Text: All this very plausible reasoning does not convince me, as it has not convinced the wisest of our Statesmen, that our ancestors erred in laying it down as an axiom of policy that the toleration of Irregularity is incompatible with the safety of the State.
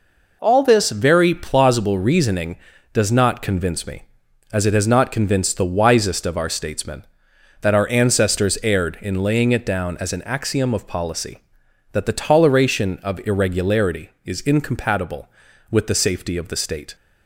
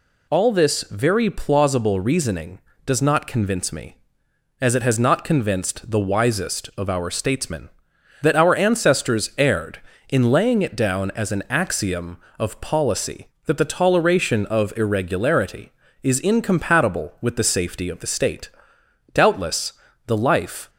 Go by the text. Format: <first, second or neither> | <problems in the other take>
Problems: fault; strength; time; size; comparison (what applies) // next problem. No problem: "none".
first | goes on to say "Doubtless the life"; from 19.1 s on; 1.5 s long